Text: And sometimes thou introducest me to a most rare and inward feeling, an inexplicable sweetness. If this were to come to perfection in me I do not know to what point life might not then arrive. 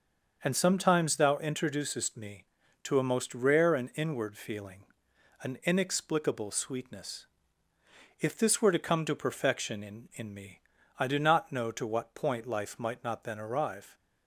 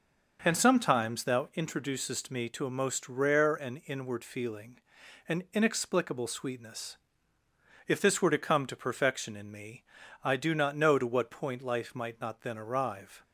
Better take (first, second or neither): second